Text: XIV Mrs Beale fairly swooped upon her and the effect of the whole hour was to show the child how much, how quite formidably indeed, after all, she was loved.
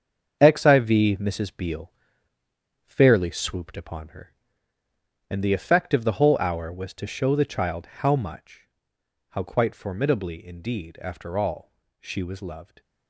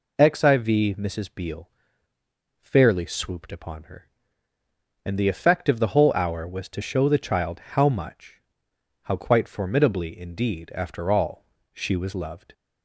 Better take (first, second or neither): second